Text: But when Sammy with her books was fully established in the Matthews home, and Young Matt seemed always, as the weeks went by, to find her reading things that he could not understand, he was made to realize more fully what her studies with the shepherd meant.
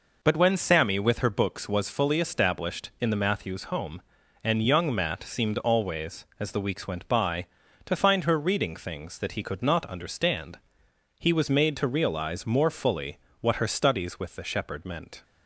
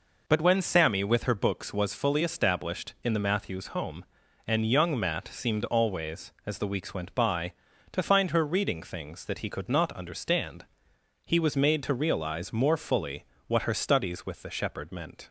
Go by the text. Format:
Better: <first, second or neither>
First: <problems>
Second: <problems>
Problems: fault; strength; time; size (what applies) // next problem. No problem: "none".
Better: neither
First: pauses between "fully" and "what"; slight; at 13.1 s; 0.22 s long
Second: pauses between "fully" and "what"; slight; at 13.2 s; 0.22 s long